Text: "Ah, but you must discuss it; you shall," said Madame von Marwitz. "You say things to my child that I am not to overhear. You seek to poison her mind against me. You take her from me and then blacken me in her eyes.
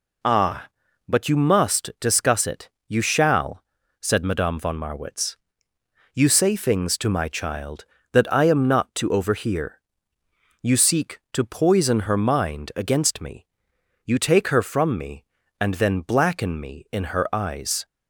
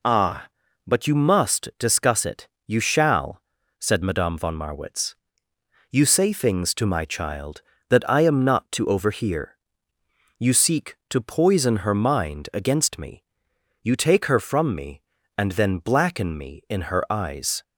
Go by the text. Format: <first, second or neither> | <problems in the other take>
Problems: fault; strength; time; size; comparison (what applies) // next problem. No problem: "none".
neither | none